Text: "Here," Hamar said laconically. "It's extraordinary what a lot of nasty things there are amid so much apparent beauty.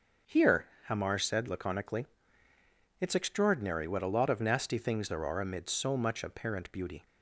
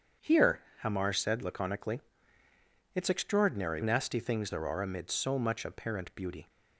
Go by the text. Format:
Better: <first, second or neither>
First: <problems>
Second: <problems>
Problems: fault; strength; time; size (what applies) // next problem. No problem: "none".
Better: first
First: starts louder than the rest; until 1.4 s; 6.5 dB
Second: starts louder than the rest; strong; until 1.4 s; 7.5 dB // skips "what a lot of"; at 3.8 s